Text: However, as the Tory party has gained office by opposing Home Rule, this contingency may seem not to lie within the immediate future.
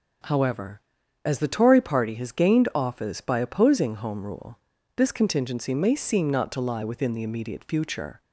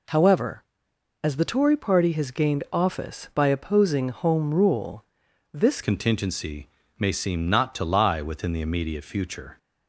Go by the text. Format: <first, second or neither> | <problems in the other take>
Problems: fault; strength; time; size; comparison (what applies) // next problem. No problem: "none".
first | changes voice at "contingency"; from 5.8 s on; 3.7 s long // pauses between "contingency" and "may"; slight; at 6.6 s; 0.28 s long